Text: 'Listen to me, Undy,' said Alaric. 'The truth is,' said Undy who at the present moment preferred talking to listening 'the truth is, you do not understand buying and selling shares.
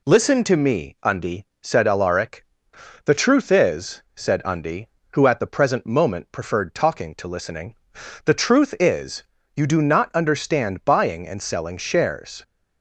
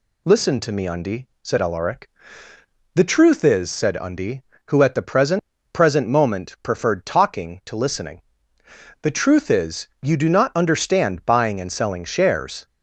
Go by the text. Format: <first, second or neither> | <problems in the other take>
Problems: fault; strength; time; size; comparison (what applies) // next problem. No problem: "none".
first | says "present" twice; at 5.7 s // pauses between "listening" and "the"; noticeable; at 8.2 s; 0.80 s long; noticeable in the first